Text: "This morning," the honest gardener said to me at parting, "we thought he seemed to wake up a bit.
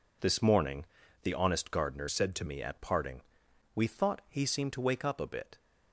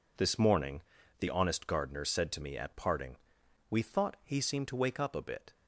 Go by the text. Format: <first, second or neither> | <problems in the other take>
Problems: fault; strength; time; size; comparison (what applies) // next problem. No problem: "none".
second | changes voice from "said" to "to"; from 2.0 to 2.4 s; 0.4 s long